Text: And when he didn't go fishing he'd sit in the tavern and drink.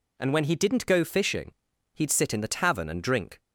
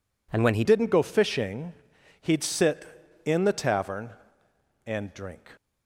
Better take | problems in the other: first | changes voice at "didn't"; from 0.6 s on; 4.8 s long // pauses between "fishing" and "he'd"; noticeable; at 1.7 s; 0.48 s long; also in the first

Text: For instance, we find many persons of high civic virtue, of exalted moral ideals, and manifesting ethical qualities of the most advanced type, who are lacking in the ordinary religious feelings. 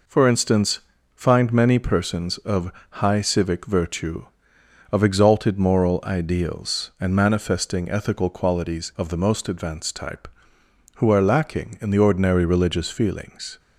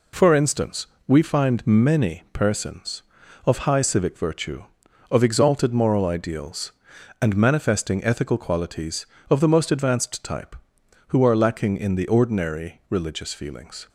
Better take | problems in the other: second | skips "we"; at 0.9 s // pauses between "of" and "high"; slight; at 2.7 s; 0.20 s long

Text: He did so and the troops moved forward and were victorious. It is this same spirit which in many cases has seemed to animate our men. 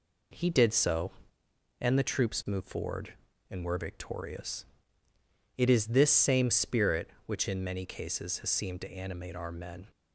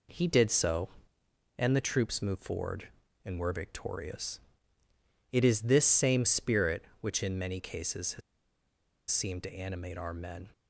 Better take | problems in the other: first | pauses between "has" and "seemed"; noticeable; at 8.2 s; 0.90 s long

